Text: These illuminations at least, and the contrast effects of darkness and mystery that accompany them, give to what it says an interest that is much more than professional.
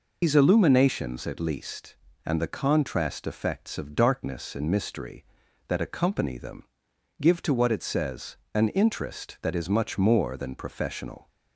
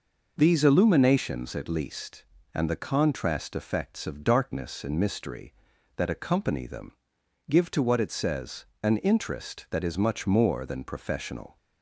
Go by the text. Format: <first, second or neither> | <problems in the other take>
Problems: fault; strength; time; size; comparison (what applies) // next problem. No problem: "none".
second | loses the start of "These"; at 0.2 s; 125 ms // pauses between "says" and "an"; slight; at 8.3 s; 0.16 s long; slight in the second